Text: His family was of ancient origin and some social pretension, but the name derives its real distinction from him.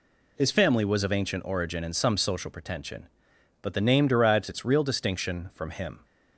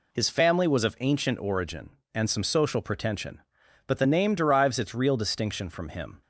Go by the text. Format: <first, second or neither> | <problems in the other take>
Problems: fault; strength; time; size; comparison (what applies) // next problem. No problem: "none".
neither | none